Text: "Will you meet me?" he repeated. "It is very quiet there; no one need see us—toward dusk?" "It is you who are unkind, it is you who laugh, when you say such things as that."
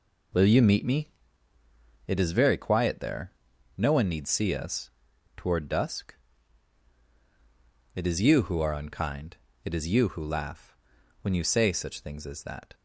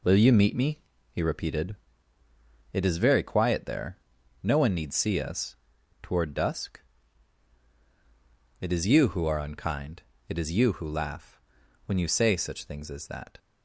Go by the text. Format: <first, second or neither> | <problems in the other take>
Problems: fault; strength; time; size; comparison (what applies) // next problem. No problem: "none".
second | skips "he repeated"; at 1.5 s